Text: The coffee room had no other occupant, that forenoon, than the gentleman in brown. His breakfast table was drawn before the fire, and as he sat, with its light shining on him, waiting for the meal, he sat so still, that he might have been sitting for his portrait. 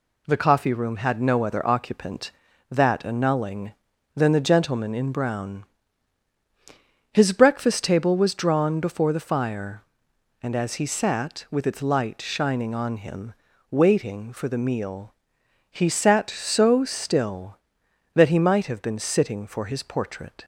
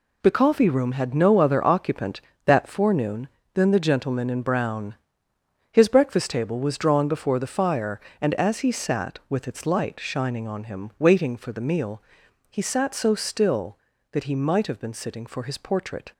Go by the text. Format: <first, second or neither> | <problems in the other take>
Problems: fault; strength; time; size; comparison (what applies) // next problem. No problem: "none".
second | says "annulling" for "forenoon"; at 3.0 s